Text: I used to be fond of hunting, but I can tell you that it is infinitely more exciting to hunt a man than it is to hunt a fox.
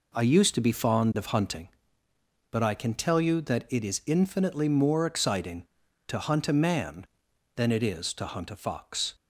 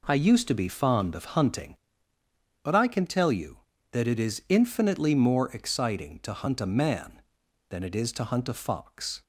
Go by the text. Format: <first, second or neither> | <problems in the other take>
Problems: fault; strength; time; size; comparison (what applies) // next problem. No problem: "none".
neither | none